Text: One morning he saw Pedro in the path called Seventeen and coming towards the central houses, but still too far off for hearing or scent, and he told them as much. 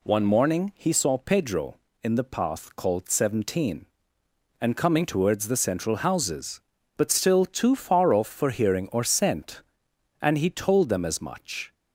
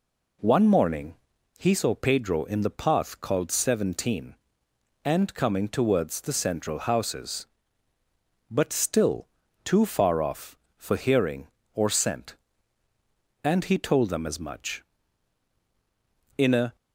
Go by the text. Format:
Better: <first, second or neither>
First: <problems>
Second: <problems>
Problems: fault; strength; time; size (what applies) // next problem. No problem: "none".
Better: first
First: none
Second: pauses between "morning" and "he"; at 1.1 s; 0.42 s long // pauses between "still" and "too"; at 9.2 s; 0.38 s long // goes on to say "In a"; slight; from 16.3 s on; 0.38 s long